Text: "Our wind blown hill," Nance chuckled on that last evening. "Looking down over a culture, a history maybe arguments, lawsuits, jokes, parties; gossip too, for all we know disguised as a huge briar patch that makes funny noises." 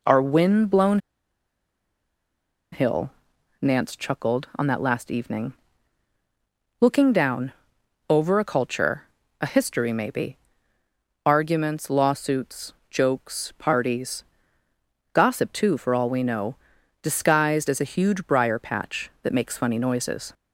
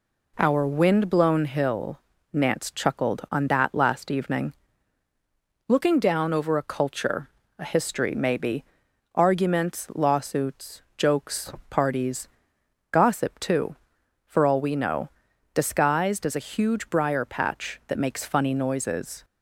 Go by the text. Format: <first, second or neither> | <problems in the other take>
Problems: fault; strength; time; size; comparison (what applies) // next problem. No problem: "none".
second | pauses between "blown" and "hill"; strong; at 0.9 s; 1.7 s long // pauses between "down" and "over"; noticeable; at 7.5 s; 0.56 s long // pauses between "maybe" and "arguments"; noticeable; at 10.3 s; 0.88 s long; noticeable in the second // pauses between "know" and "disguised"; noticeable; at 16.5 s; 0.46 s long; noticeable in the second